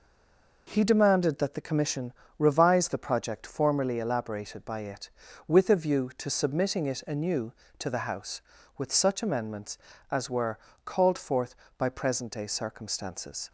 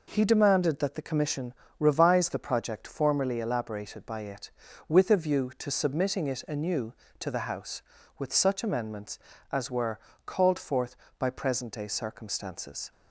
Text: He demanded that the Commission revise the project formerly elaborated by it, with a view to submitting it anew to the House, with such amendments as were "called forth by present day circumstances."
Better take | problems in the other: second | stays silent before the first word; slight; until 0.6 s; 0.6 s long // pauses between "Commission" and "revise"; slight; at 2.1 s; 0.26 s long; slight in the second // pauses between "were" and "called"; slight; at 10.5 s; 0.26 s long; slight in the second

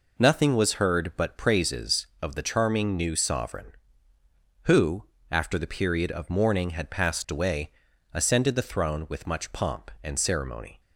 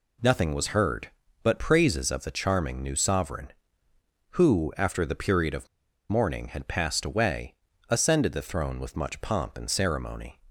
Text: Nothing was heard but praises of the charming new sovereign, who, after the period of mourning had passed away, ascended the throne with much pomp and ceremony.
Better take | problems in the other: first | pauses between "of" and "mourning"; at 5.6 s; 0.44 s long

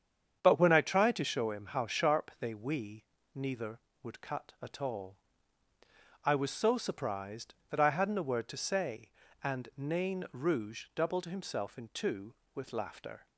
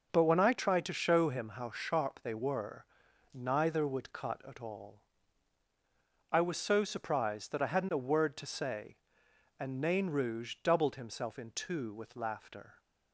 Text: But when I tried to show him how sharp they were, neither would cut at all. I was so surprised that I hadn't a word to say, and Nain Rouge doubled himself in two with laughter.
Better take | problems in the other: second | starts louder than the rest; strong; until 1.4 s; 8 dB // says "we" for "were"; at 2.5 s

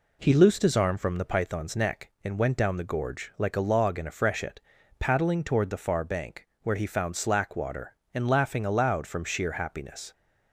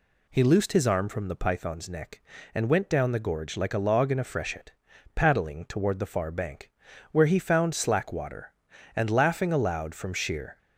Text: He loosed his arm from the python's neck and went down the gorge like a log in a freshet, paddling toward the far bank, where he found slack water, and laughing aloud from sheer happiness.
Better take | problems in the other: first | stops before "happiness"; at 10.5 s

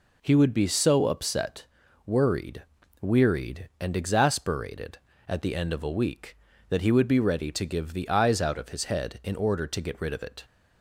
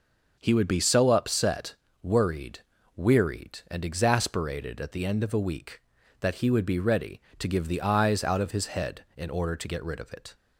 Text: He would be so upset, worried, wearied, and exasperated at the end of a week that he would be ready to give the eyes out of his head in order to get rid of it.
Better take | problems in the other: neither | none

